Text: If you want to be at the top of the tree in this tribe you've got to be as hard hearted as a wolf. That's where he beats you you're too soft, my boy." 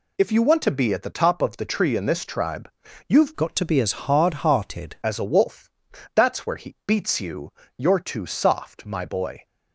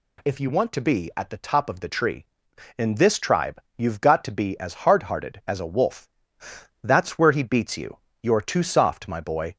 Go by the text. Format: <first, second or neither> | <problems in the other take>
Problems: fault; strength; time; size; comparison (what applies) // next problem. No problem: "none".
second | pauses between "tribe" and "you've"; at 2.7 s; 0.38 s long; slight in the second // changes voice from "got" to "hearted"; from 3.3 to 4.9 s; 1.6 s long // pauses between "you" and "you're"; slight; at 7.5 s; 0.24 s long; slight in the second